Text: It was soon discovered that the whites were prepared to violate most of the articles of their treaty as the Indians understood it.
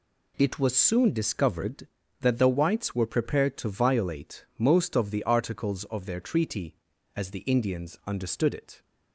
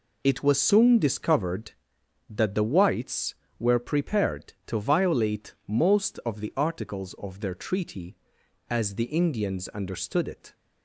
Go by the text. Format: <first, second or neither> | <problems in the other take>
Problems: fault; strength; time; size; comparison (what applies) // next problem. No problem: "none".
neither | none